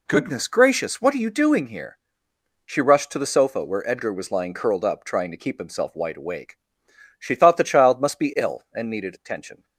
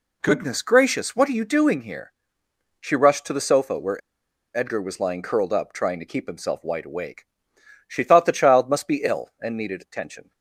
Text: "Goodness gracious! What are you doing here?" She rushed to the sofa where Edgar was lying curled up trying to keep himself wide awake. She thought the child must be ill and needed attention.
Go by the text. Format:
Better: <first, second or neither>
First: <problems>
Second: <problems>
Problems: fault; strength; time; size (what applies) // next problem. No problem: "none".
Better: first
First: none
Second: pauses between "where" and "Edgar"; noticeable; at 4.0 s; 0.57 s long